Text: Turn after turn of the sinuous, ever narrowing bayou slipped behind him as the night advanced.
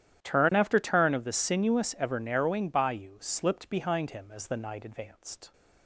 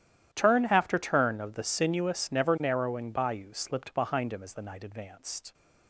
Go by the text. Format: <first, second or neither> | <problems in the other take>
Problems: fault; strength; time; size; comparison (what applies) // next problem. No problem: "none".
first | starts louder than the rest; strong; until 1.3 s; 11.5 dB; strong in the first // says "never" for "ever"; at 2.3 s